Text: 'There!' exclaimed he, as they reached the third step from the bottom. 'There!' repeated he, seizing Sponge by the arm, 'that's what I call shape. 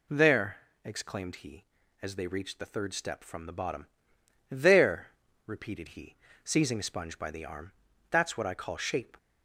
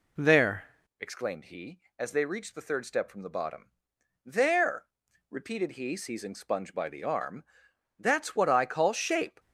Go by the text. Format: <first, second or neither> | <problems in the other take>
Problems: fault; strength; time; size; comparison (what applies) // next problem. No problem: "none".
first | changes voice at "exclaimed"; from 0.9 s on; 8.4 s long